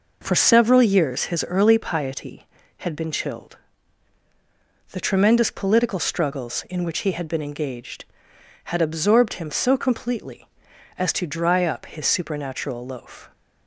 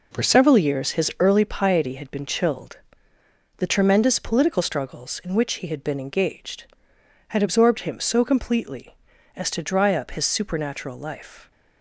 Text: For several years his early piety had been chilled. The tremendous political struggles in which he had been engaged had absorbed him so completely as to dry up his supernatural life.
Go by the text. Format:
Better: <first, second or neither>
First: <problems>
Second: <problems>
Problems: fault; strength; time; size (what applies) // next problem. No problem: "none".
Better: second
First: says "loaf" for "life"; at 12.8 s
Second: none